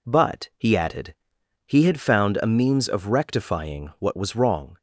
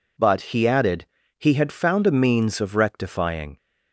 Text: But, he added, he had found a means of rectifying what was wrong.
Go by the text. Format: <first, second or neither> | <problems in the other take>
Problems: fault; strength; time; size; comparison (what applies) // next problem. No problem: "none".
first | stops before "what was wrong"; at 3.5 s